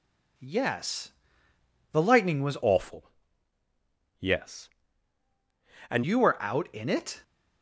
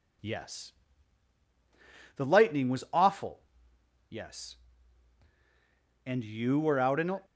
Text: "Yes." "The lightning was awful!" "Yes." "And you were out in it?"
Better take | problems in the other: second | changes voice from "awful" to "And"; from 2.6 to 6.0 s; 3.4 s long

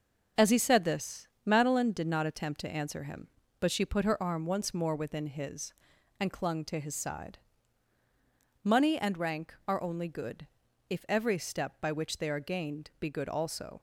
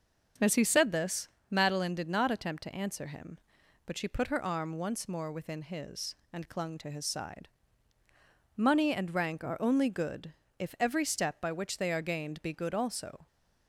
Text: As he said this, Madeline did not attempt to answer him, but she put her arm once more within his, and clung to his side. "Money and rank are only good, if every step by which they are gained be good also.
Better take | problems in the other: neither | starts louder than the rest; the same in both

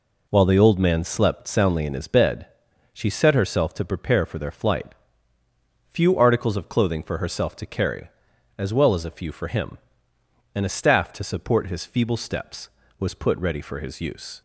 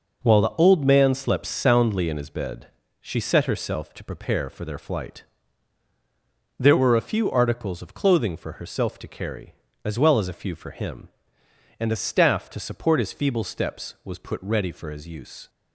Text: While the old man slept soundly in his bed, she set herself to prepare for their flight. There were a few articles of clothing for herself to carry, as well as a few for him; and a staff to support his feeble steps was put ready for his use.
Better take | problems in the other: second | skips "There were a"; at 5.4 s

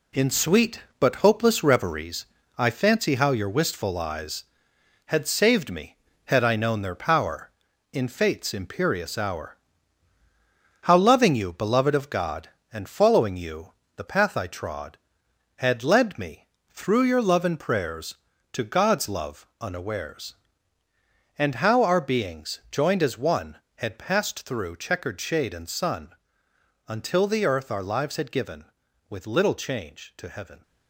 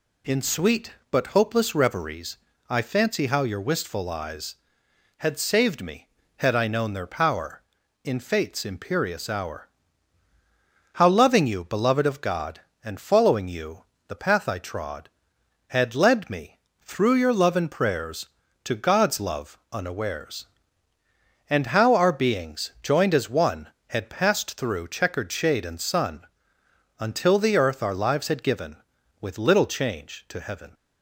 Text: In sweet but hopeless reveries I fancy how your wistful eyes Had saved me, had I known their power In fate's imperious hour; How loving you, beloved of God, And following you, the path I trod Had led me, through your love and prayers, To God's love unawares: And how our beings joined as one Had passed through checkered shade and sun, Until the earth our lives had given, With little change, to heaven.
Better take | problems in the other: second | gets quieter; throughout; 6.5 dB // pauses between "reveries" and "I"; slight; at 2.2 s; 0.30 s long; slight in the second

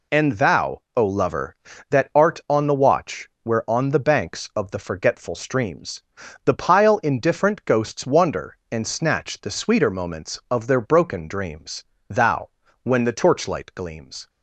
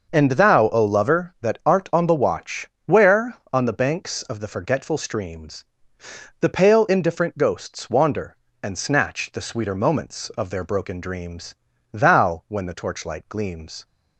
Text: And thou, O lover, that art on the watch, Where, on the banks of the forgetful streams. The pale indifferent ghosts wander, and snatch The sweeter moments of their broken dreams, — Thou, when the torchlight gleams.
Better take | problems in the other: second | says "pile" for "pale"; at 6.5 s

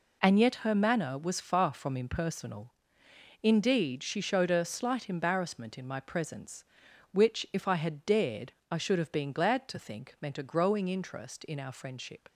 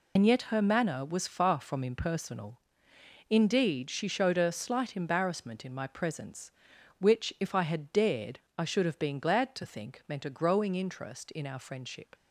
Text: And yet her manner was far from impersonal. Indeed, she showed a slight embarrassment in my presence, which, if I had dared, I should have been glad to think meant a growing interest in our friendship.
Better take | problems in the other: first | loses the start of "And"; at 0.1 s; 70 ms

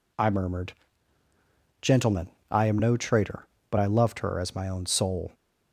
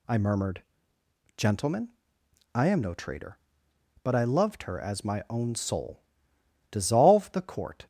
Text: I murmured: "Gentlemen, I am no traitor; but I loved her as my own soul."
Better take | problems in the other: first | goes on to say "Dissolve the Court"; noticeable; from 6.7 s on; 1.1 s long

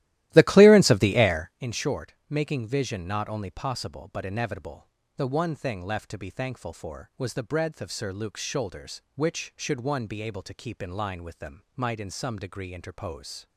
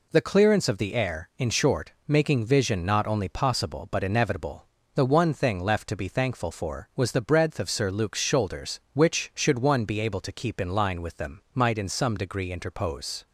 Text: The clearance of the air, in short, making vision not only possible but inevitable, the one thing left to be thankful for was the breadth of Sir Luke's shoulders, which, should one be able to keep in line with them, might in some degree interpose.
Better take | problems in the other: second | starts louder than the rest; strong; until 1.6 s; 15 dB

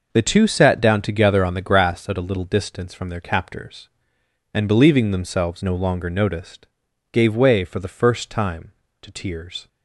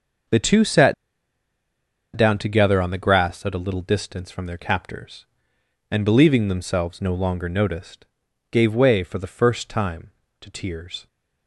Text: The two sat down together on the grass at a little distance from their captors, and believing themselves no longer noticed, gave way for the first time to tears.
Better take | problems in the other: first | pauses between "sat" and "down"; at 0.9 s; 1.2 s long

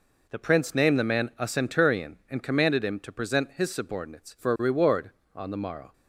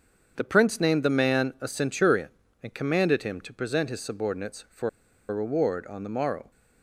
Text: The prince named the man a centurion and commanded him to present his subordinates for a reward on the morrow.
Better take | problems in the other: first | starts louder than the rest; strong; until 1.3 s; 7.5 dB // pauses between "for" and "a"; at 4.8 s; 0.40 s long

